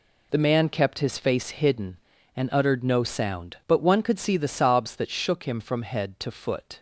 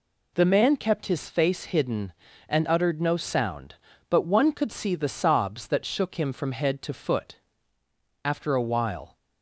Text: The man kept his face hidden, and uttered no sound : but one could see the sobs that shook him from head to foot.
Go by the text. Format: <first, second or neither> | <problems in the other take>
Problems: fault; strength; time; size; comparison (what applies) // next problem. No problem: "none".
first | goes on to say "After a while"; noticeable; from 8.2 s on; 0.94 s long